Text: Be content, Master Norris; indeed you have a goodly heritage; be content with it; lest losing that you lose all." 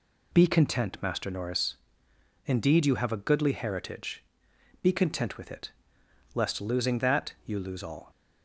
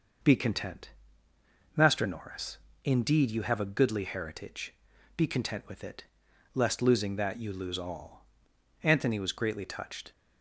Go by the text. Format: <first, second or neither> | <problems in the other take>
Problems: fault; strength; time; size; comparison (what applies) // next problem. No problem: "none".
first | goes on to say "Anthony was greatly touched"; noticeable; from 8.8 s on; 1.2 s long